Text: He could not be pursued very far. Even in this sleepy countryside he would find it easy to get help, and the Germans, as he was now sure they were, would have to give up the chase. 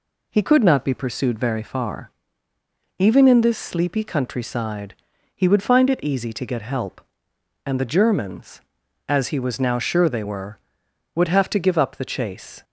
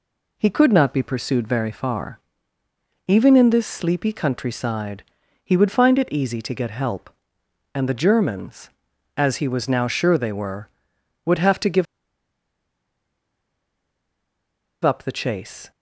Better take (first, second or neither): first